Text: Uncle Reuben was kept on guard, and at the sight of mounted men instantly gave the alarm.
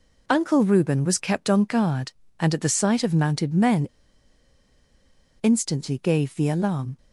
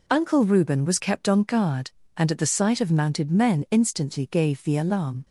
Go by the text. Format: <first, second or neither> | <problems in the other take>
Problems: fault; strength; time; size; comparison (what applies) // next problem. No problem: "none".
second | pauses between "men" and "instantly"; strong; at 3.8 s; 1.5 s long